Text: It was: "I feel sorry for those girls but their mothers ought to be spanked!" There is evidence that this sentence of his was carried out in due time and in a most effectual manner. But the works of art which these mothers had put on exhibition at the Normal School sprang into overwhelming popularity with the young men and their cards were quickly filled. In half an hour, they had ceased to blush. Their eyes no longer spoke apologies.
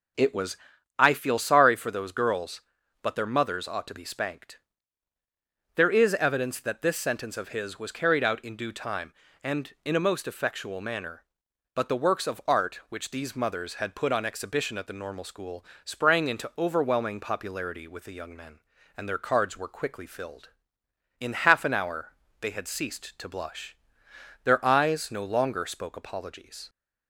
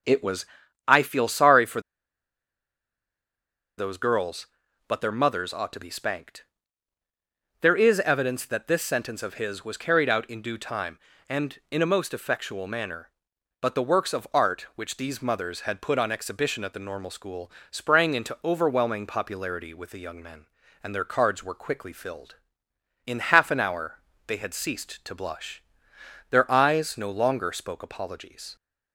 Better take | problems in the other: first | pauses between "for" and "those"; strong; at 1.7 s; 1.9 s long // pauses between "School" and "sprang"; slight; at 17.5 s; 0.18 s long; slight in the first

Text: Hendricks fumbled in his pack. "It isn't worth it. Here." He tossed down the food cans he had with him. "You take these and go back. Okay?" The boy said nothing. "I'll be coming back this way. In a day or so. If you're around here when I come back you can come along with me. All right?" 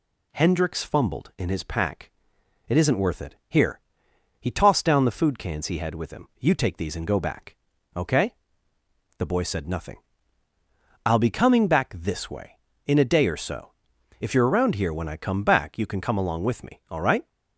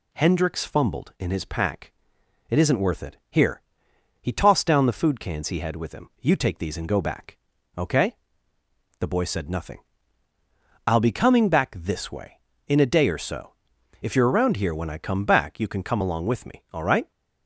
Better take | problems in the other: neither | none

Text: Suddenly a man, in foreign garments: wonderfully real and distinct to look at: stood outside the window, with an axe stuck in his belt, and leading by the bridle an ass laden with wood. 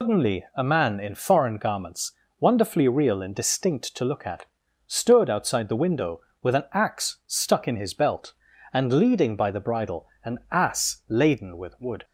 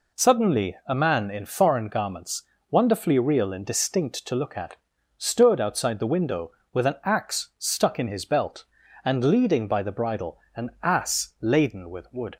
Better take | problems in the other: second | loses the start of "Suddenly"; at 0.0 s; 170 ms // pauses between "bridle" and "an"; slight; at 10.0 s; 0.16 s long; slight in the second

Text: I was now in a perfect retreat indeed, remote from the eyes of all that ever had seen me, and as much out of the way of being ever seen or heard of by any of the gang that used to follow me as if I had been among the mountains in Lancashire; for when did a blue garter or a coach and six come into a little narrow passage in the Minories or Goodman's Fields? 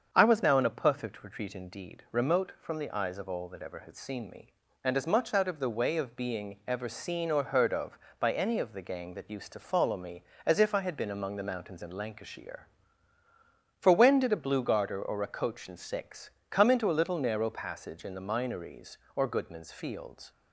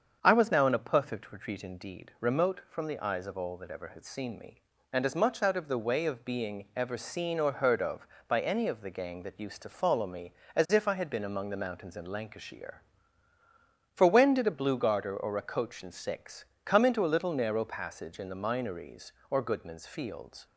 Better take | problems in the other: neither | starts louder than the rest; strong; the same in both // pauses between "six" and "come"; slight; the same in both

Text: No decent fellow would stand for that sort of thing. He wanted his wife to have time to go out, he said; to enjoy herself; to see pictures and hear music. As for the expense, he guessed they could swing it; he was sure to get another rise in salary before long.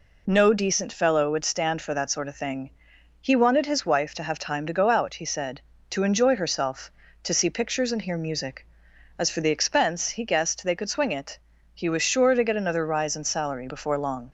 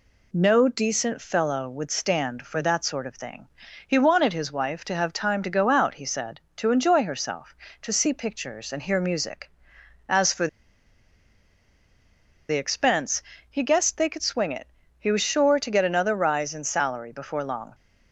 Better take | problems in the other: first | pauses between "for" and "the"; strong; at 10.4 s; 2.0 s long

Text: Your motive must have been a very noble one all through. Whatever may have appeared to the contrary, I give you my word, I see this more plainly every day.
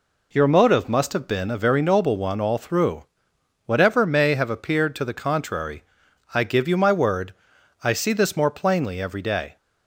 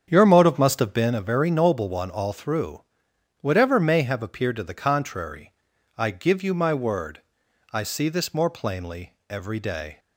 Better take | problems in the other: first | starts louder than the rest; strong; until 1.2 s; 8 dB // pauses between "plainly" and "every"; slight; at 9.1 s; 0.16 s long

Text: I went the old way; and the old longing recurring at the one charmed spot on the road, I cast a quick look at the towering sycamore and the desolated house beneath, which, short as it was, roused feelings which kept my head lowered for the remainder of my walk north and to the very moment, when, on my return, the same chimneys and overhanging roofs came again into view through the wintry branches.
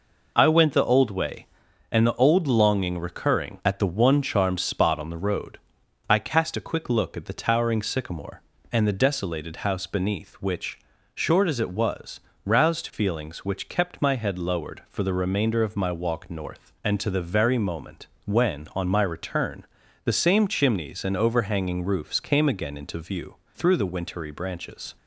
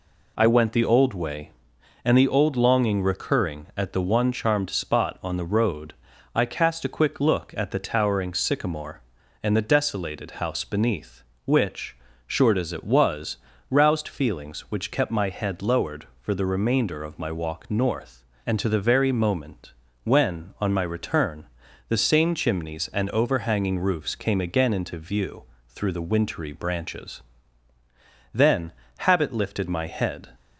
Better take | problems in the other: first | pauses between "view" and "through"; slight; at 25.4 s; 0.26 s long; slight in the first // goes on to say "Then habit lifted my head"; strong; from 28.3 s on; 1.9 s long

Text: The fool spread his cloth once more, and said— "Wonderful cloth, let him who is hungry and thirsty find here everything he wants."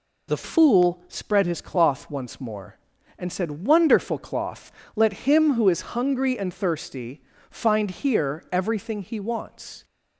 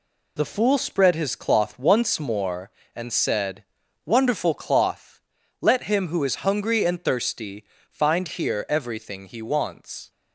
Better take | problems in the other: second | changes voice at "fool"; from 0.4 s on; 9.4 s long // pauses between "thirsty" and "find"; slight; at 7.2 s; 0.30 s long; slight in the second

